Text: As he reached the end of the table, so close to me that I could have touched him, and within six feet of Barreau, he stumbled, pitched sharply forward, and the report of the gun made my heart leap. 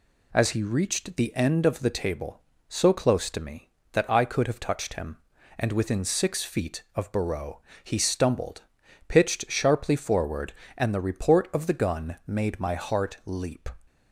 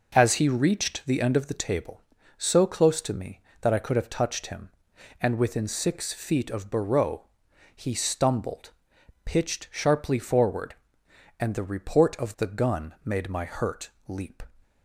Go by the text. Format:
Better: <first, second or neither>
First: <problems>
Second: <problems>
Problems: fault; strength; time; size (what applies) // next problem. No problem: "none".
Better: first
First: none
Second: says "hurt" for "heart"; at 13.4 s